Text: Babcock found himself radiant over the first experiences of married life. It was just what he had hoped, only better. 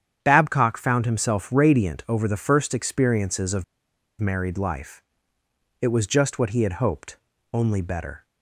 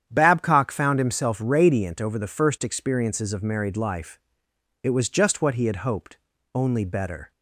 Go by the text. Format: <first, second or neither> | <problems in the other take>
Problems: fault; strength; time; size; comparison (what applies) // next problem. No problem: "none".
second | starts louder than the rest; strong; until 1.2 s; 9 dB; strong in the second // pauses between "of" and "married"; noticeable; at 3.6 s; 0.54 s long